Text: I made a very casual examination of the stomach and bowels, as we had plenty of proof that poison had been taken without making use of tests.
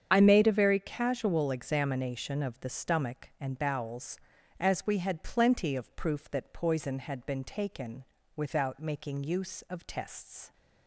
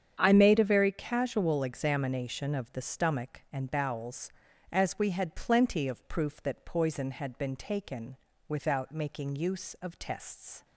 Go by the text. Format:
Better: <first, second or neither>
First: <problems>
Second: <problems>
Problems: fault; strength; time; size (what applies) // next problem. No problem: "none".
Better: second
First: loses the start of "I"; at 0.1 s; 55 ms // starts louder than the rest; strong; until 1.1 s; 8 dB // pauses between "taken" and "without"; slight; at 8.0 s; 0.32 s long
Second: starts louder than the rest; strong; until 1.2 s; 8 dB // pauses between "taken" and "without"; slight; at 8.1 s; 0.32 s long